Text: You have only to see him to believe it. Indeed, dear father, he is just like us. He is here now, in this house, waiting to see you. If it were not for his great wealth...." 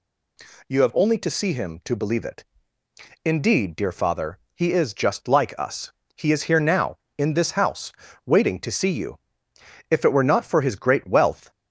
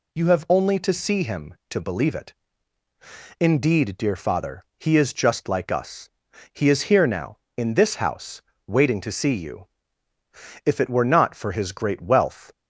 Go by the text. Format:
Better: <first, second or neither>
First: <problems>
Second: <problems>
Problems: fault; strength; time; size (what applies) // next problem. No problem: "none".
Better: neither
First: none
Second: none